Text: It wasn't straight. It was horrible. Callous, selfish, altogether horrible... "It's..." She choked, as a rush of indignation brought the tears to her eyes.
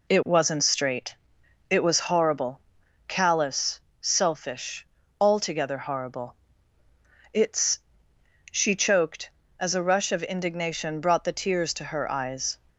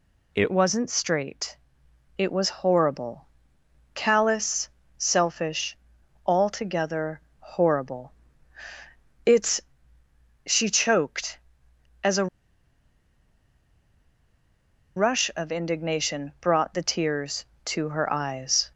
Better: first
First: none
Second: pauses between "altogether" and "horrible"; slight; at 7.2 s; 0.20 s long // pauses between "a" and "rush"; strong; at 12.2 s; 2.6 s long

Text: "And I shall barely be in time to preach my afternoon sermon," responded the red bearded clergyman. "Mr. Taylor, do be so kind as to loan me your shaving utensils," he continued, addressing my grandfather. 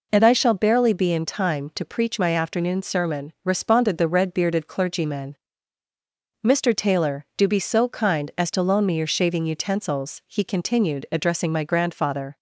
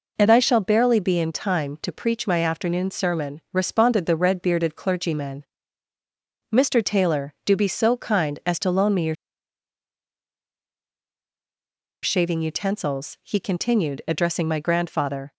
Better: first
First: none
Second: pauses between "your" and "shaving"; strong; at 9.1 s; 2.8 s long

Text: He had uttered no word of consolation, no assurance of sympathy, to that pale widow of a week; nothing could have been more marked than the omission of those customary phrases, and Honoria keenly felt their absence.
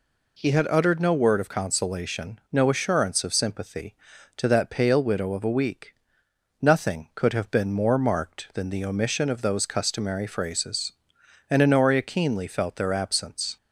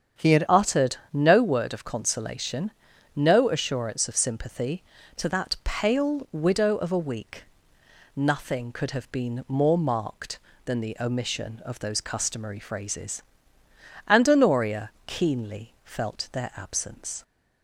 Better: first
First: none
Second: starts louder than the rest; strong; until 1.3 s; 8 dB // changes voice at "uttered"; from 0.4 s on; 16.8 s long // pauses between "uttered" and "no"; slight; at 0.9 s; 0.16 s long // pauses between "Honoria" and "keenly"; slight; at 14.9 s; 0.16 s long

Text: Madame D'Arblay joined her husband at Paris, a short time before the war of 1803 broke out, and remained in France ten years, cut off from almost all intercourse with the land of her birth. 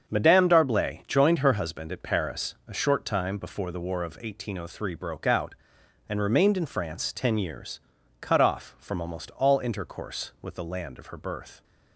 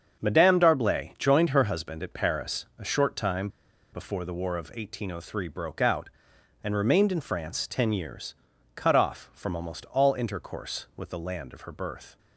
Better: first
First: starts louder than the rest; strong; until 1.1 s; 7.5 dB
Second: starts louder than the rest; strong; until 1.2 s; 7.5 dB // pauses between "time" and "before"; at 3.4 s; 0.44 s long

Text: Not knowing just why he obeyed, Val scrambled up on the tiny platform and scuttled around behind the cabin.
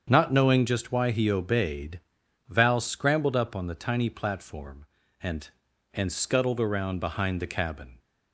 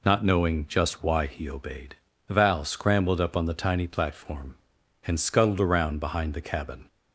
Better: second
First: starts louder than the rest; strong; until 1.1 s; 7.5 dB // says "and" twice; at 5.9 s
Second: none

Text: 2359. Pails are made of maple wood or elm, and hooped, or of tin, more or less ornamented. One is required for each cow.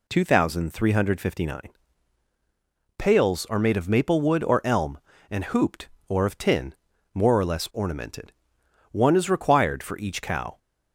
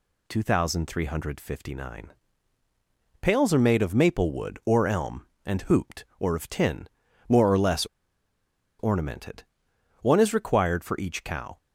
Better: first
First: none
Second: pauses between "less" and "ornamented"; noticeable; at 7.8 s; 0.93 s long

